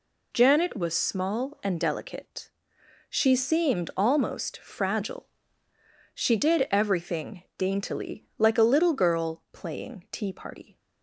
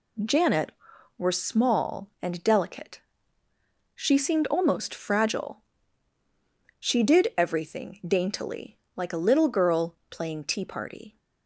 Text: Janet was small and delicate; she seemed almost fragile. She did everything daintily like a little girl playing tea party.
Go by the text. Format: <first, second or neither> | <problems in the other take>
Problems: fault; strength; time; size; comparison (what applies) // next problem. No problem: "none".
first | says "were" for "was"; at 1.1 s // pauses between "daintily" and "like"; slight; at 8.7 s; 0.18 s long